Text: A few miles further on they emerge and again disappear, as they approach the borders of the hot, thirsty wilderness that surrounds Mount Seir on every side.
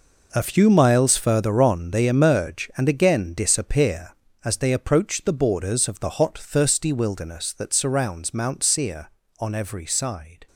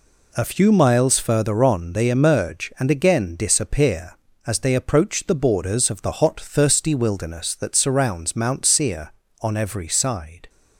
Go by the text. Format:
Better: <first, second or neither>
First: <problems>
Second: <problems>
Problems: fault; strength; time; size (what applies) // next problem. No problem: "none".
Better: second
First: gets quieter; strong; throughout; 12 dB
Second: none